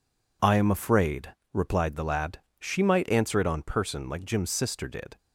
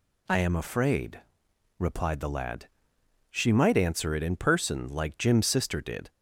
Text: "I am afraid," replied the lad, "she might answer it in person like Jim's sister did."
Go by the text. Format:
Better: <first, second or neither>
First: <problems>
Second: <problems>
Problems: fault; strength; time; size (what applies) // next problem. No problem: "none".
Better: second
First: says "on" for "in"; at 3.4 s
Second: none